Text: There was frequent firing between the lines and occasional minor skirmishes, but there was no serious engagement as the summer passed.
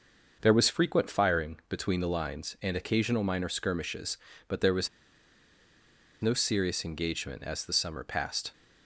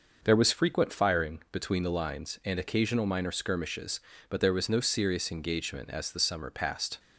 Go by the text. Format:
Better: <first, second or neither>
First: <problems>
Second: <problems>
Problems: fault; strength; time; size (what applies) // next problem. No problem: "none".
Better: second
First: starts louder than the rest; noticeable; until 1.4 s; 6 dB // pauses between "was" and "no"; strong; at 4.8 s; 1.3 s long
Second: starts louder than the rest; noticeable; until 1.2 s; 6 dB